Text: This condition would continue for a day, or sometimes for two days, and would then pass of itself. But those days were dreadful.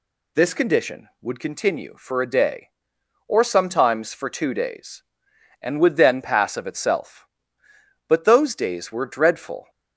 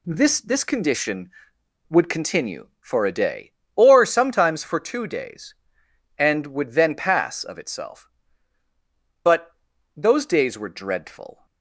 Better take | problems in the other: first | says "This" twice; at 0.3 s // pauses between "But" and "those"; at 9.5 s; 0.44 s long

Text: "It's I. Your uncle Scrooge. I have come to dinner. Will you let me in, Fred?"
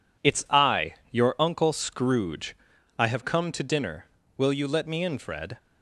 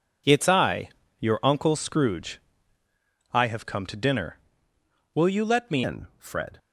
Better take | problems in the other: first | changes voice at "in"; from 5.8 s on; 0.7 s long

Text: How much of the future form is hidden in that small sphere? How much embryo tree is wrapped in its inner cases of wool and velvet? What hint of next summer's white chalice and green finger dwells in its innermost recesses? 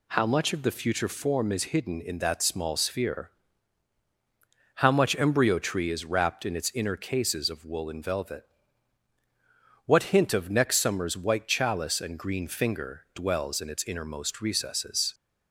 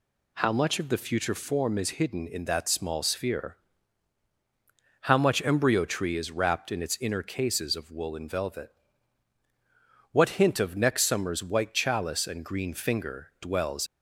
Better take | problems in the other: first | stops before "in its innermost recesses"; at 13.8 s

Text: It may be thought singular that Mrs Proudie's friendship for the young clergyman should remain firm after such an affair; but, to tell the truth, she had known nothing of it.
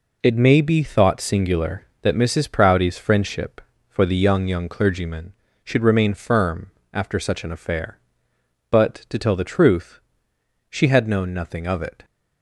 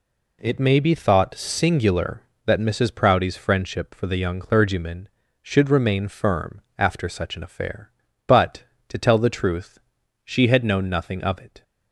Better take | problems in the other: second | says "young" twice; at 4.4 s // pauses between "firm" and "after"; slight; at 6.7 s; 0.22 s long; slight in the second

